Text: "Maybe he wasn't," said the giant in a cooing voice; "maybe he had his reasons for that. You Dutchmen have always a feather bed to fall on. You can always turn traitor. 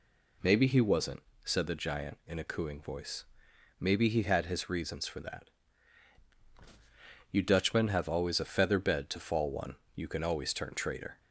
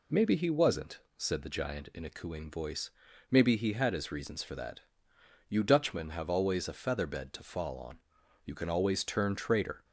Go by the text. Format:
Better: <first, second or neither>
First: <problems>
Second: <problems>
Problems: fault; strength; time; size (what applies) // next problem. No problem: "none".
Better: second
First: says "one" for "on"; at 9.5 s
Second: none